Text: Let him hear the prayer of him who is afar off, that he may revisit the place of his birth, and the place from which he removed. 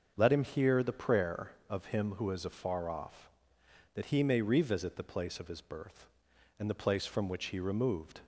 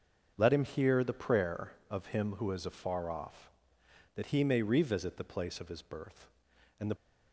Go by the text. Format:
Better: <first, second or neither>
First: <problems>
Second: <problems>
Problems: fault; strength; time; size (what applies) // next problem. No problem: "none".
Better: first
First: starts louder than the rest; until 1.1 s; 6.5 dB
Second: starts louder than the rest; until 1.3 s; 6.5 dB // stops before "place from which he removed"; at 6.9 s